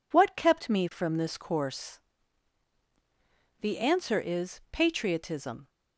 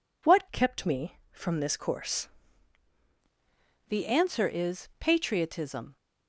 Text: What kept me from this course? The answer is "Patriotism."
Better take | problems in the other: first | changes voice from "kept" to "course"; from 0.5 to 2.2 s; 1.7 s long

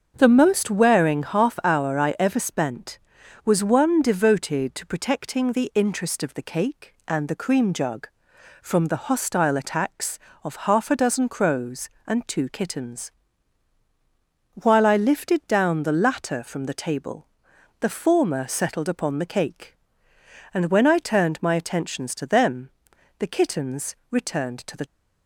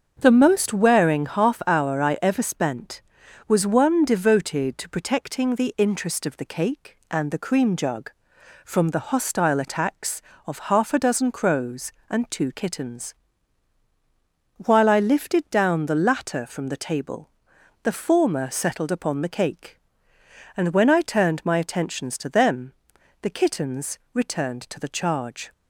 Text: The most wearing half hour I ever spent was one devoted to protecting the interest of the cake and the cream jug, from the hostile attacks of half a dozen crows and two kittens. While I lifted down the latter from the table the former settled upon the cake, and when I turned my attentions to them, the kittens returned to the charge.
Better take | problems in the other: second | starts louder than the rest; until 1.1 s; 6.5 dB; also in the second // pauses between "table" and "the"; noticeable; at 17.2 s; 0.54 s long; noticeable in the second // stops before "charge"; at 24.8 s

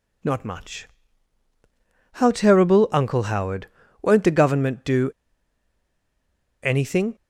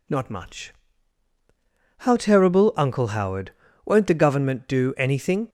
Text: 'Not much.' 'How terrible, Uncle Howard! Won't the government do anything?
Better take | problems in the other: second | pauses between "do" and "anything"; strong; at 5.0 s; 1.5 s long

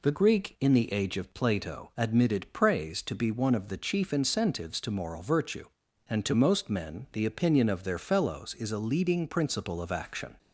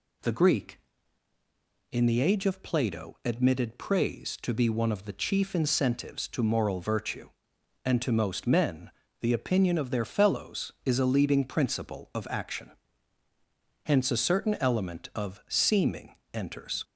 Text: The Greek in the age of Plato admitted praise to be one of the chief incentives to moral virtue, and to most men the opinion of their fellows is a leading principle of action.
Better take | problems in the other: first | pauses between "men" and "the"; slight; at 8.9 s; 0.30 s long // goes on to say "Hence a certain element of seeming enters"; strong; from 13.8 s on; 3.0 s long

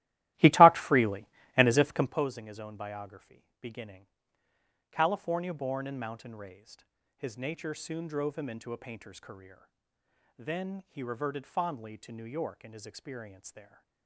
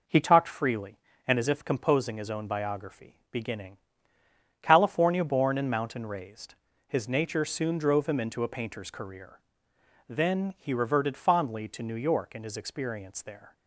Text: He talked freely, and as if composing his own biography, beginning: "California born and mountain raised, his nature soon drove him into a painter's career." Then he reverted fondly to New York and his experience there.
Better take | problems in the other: second | starts louder than the rest; strong; until 2.3 s; 16 dB

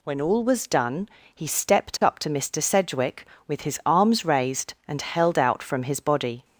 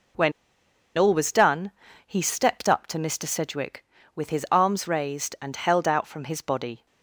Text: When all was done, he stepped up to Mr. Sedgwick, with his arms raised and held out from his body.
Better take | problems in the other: first | pauses between "When" and "all"; noticeable; at 0.3 s; 0.65 s long

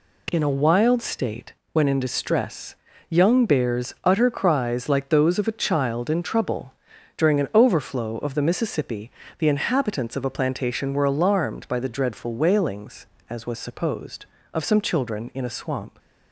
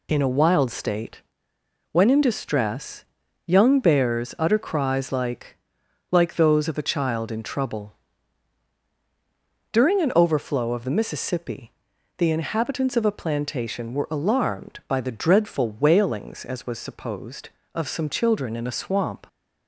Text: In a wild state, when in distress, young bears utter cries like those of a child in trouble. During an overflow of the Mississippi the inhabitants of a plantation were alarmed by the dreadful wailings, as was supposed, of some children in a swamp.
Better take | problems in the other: first | says "like" twice; at 6.1 s // pauses between "Mississippi" and "the"; at 11.7 s; 0.44 s long; slight in the first

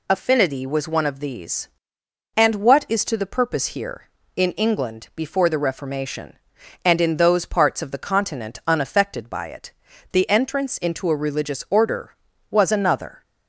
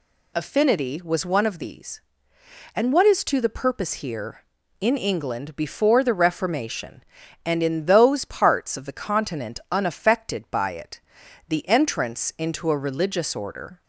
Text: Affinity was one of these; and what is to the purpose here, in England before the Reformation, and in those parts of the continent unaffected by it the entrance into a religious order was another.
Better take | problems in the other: first | pauses between "it" and "the"; noticeable; at 10.9 s; 0.48 s long; also in the first // stops before "was another"; at 13.8 s

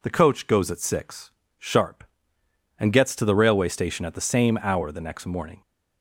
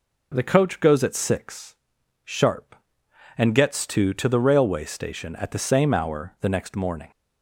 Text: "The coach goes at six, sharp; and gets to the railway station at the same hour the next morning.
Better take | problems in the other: first | says "to" twice; at 4.1 s

